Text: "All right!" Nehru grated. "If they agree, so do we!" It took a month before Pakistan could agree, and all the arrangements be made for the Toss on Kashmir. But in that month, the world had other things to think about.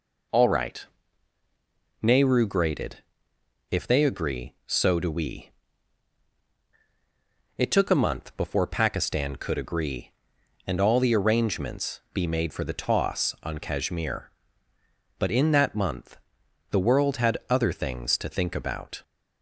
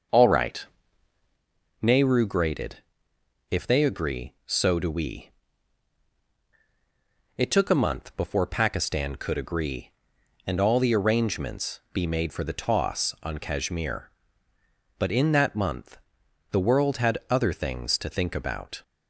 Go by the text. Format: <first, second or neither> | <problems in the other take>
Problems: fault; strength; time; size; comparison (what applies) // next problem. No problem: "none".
first | starts louder than the rest; noticeable; until 1.4 s; 6 dB